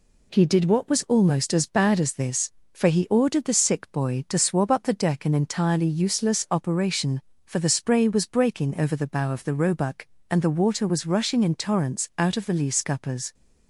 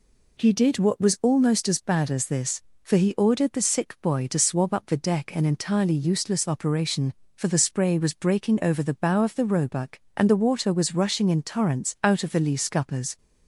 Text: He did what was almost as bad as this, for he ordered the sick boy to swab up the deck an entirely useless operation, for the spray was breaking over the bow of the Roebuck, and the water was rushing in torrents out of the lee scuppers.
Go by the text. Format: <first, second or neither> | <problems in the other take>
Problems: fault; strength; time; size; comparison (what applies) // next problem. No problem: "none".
neither | none